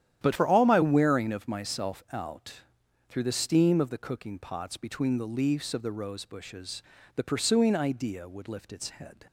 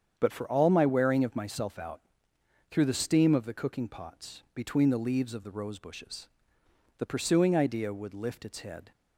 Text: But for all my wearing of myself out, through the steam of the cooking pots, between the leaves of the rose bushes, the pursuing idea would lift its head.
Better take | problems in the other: second | starts louder than the rest; strong; until 1.2 s; 10.5 dB; strong in the second // changes voice from "for" to "my"; from 0.3 to 0.8 s; 0.5 s long

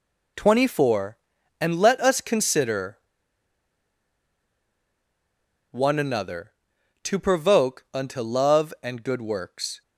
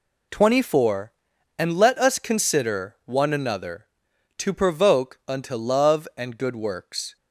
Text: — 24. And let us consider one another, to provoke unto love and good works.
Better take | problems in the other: second | pauses between "consider" and "one"; strong; at 2.9 s; 2.7 s long

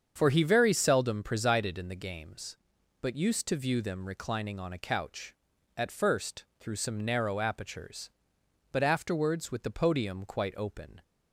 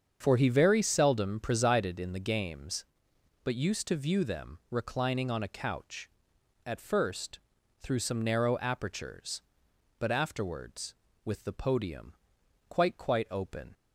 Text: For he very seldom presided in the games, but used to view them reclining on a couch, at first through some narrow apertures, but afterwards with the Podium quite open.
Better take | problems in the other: first | starts louder than the rest; strong; until 1.2 s; 7.5 dB; also in the first // pauses between "first" and "through"; at 7.3 s; 0.40 s long // pauses between "Podium" and "quite"; noticeable; at 12.1 s; 0.56 s long // says "quite" twice; at 12.9 s

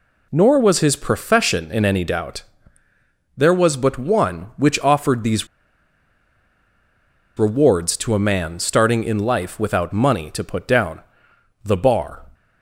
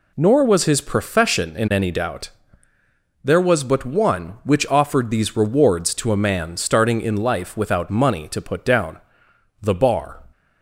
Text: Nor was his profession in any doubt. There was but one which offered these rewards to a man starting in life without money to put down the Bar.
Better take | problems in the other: second | pauses between "these" and "rewards"; strong; at 5.4 s; 1.9 s long // pauses between "down" and "the"; noticeable; at 11.0 s; 0.62 s long; noticeable in the second

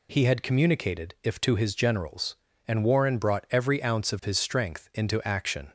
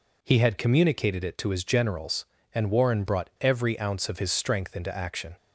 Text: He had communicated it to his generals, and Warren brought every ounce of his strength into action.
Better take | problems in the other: second | says "if" for "it"; at 1.2 s

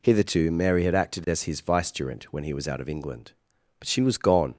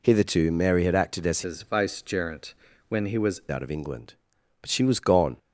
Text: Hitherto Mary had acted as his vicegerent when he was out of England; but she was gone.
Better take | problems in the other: first | changes voice from "his" to "was"; from 1.4 to 3.3 s; 1.9 s long // pauses between "vicegerent" and "when"; at 2.5 s; 0.38 s long

